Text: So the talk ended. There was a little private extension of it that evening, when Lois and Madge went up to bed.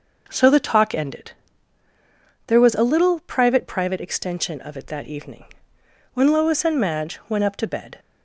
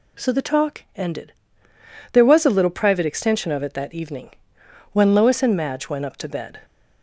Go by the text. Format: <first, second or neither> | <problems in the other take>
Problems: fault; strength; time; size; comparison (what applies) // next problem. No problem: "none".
second | says "private" twice; at 3.6 s